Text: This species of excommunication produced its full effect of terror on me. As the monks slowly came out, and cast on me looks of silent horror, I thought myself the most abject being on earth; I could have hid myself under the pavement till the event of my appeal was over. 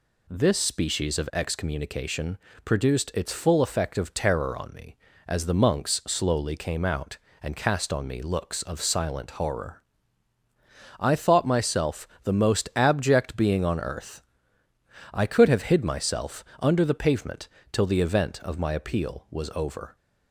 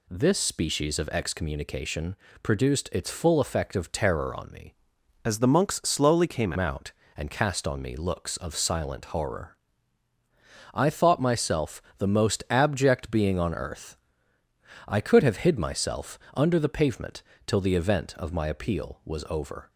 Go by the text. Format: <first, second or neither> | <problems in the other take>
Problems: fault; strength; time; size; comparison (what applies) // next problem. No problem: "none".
first | pauses between "excommunication" and "produced"; slight; at 2.1 s; 0.26 s long; slight in the first // changes voice from "As" to "came"; from 5.2 to 6.5 s; 1.3 s long // pauses between "myself" and "the"; slight; at 11.8 s; 0.16 s long; slight in the first // pauses between "pavement" and "till"; slight; at 17.2 s; 0.24 s long; slight in the first